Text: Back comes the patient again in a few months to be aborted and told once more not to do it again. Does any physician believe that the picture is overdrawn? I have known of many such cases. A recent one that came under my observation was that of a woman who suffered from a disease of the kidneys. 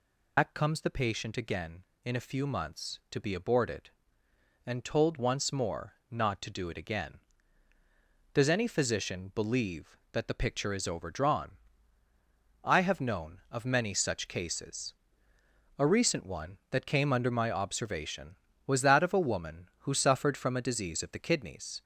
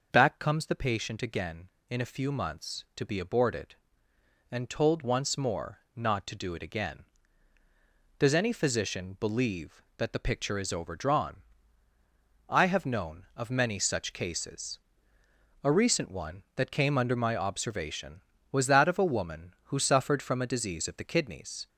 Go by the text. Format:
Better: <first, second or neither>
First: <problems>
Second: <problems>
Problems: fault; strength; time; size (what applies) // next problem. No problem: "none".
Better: second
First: loses the start of "Back"; at 0.3 s; 110 ms // pauses between "more" and "not"; slight; at 5.9 s; 0.18 s long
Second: pauses between "more" and "not"; slight; at 5.7 s; 0.18 s long